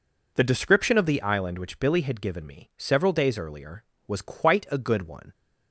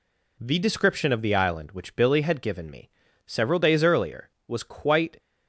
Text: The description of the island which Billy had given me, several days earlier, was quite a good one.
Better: first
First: none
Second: stops before "a good one"; at 5.1 s

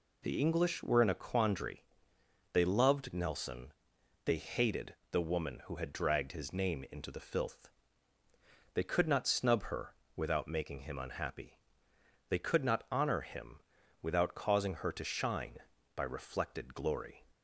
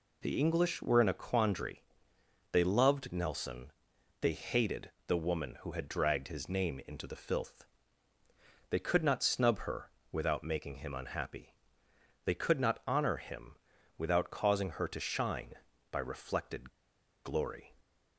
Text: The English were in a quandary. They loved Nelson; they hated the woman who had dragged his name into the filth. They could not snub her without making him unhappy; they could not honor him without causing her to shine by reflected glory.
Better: first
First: pauses between "hated" and "the"; slight; at 4.9 s; 0.18 s long // pauses between "her" and "without"; slight; at 9.9 s; 0.22 s long // pauses between "him" and "without"; at 13.6 s; 0.42 s long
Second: pauses between "hated" and "the"; slight; at 4.9 s; 0.18 s long // pauses between "her" and "without"; slight; at 9.9 s; 0.22 s long // pauses between "him" and "without"; at 13.5 s; 0.42 s long // pauses between "reflected" and "glory"; noticeable; at 16.7 s; 0.53 s long

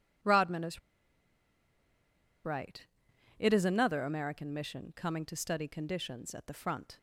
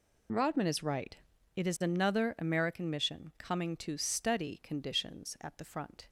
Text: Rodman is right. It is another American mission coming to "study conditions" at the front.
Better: second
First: pauses between "is" and "right"; strong; at 0.7 s; 1.6 s long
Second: none

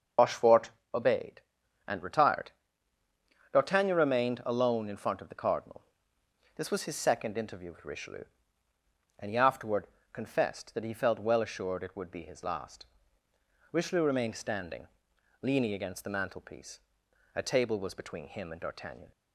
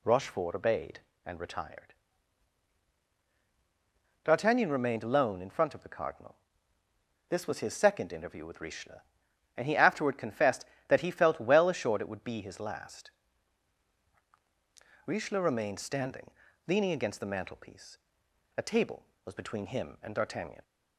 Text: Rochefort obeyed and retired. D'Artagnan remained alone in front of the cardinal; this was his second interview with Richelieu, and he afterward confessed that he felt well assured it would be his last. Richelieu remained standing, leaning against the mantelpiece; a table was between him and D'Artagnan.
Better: second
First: loses the start of "Rochefort"; at 0.1 s; 75 ms // starts louder than the rest; until 1.4 s; 6.5 dB // pauses between "Rochefort" and "obeyed"; slight; at 0.7 s; 0.22 s long // pauses between "afterward" and "confessed"; slight; at 9.8 s; 0.26 s long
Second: none

